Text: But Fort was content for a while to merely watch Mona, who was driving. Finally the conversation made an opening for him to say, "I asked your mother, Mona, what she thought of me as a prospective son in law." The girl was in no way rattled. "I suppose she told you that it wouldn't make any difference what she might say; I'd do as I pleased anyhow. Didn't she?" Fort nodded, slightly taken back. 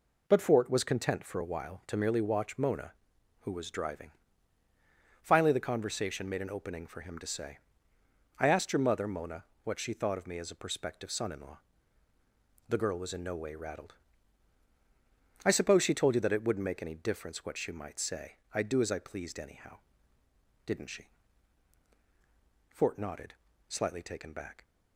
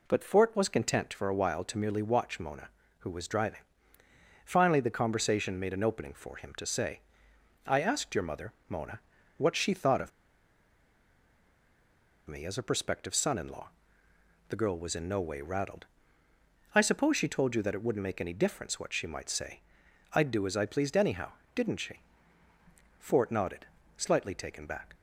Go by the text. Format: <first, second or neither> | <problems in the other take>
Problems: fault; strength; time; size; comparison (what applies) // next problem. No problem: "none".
first | pauses between "of" and "me"; strong; at 10.1 s; 2.1 s long